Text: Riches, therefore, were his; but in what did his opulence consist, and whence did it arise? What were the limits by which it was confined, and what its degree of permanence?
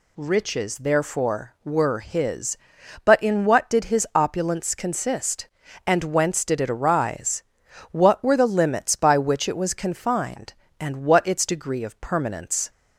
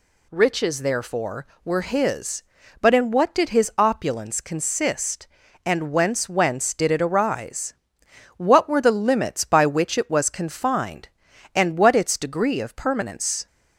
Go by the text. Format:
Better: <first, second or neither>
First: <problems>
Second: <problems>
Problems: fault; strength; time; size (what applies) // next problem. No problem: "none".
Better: first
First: none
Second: says "whence" twice; at 6.2 s